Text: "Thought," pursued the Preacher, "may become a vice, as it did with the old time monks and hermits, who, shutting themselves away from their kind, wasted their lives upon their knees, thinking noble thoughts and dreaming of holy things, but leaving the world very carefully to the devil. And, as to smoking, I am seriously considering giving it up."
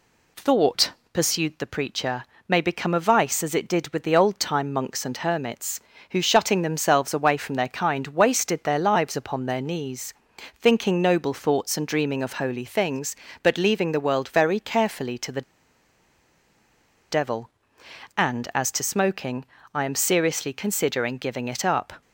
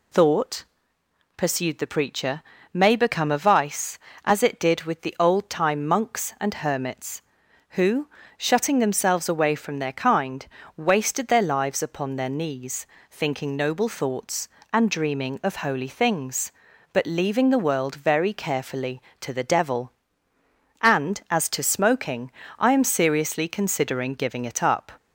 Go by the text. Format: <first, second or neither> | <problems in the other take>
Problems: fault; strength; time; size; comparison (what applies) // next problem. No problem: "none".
second | pauses between "the" and "devil"; strong; at 15.4 s; 1.6 s long